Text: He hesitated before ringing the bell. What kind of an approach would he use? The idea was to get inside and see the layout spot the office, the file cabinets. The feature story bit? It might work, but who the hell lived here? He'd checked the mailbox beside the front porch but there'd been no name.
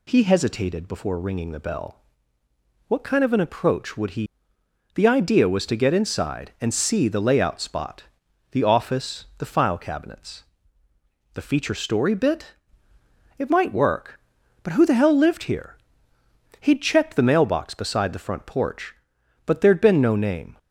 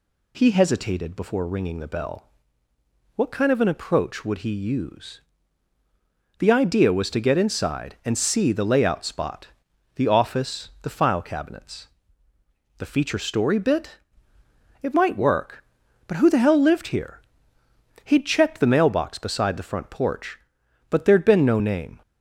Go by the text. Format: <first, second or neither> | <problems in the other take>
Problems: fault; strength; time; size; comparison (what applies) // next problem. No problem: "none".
second | skips "use"; at 4.5 s // pauses between "spot" and "the"; noticeable; at 8.0 s; 0.46 s long; noticeable in the second